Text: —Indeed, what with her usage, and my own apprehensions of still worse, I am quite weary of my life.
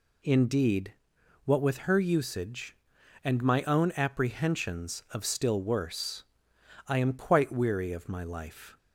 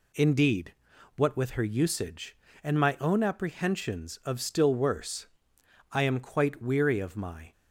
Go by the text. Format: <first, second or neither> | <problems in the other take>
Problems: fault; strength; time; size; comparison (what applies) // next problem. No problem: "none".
first | stops before "life"; at 7.5 s